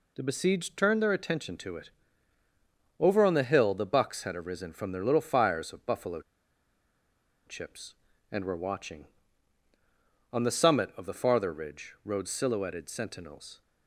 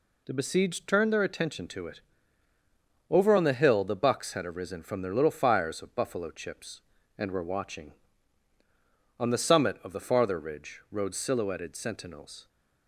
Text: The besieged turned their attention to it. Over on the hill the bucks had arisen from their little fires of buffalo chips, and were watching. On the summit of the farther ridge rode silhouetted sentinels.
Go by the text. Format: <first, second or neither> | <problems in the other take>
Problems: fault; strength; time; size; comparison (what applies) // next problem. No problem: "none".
second | pauses between "buffalo" and "chips"; strong; at 6.2 s; 1.2 s long